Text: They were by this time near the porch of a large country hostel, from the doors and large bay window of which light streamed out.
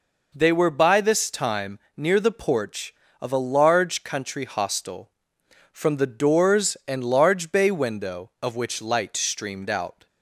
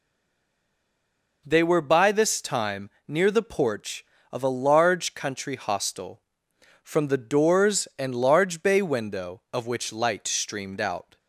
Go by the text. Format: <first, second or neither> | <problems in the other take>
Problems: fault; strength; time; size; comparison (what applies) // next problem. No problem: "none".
first | stays silent before the first word; noticeable; until 1.4 s; 1.4 s long // pauses between "time" and "near"; slight; at 2.8 s; 0.18 s long; slight in the first